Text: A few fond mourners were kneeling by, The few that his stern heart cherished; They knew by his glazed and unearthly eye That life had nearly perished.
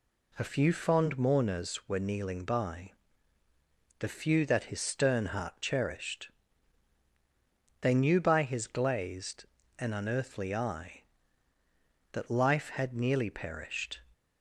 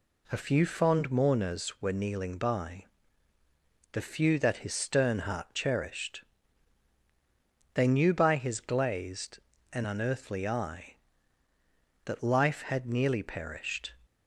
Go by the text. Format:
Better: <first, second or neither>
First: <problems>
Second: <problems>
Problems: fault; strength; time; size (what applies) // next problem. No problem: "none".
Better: neither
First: none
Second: none